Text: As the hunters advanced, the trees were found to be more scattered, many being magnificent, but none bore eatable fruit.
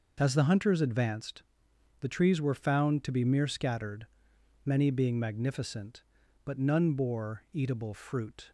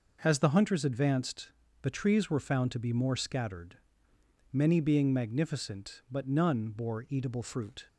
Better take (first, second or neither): second